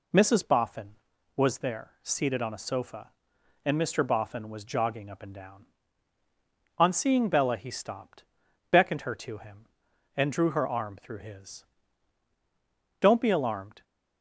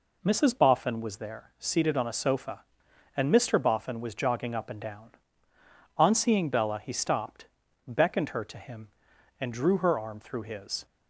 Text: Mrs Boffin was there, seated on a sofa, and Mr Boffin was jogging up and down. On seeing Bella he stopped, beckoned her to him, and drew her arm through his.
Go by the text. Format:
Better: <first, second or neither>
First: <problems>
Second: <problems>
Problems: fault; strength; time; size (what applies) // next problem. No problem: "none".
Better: second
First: goes on to say "Don't be alarmed"; noticeable; from 12.9 s on; 0.84 s long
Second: none